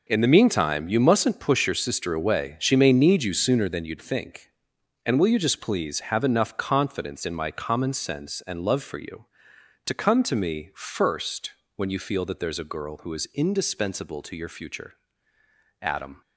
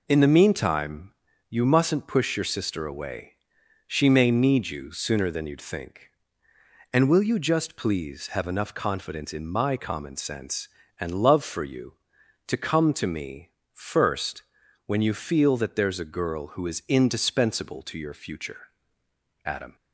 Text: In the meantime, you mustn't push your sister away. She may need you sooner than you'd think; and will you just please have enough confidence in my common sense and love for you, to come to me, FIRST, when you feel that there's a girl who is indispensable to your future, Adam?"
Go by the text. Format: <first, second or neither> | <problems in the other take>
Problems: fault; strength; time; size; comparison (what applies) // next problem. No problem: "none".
second | gets quieter; strong; throughout; 11 dB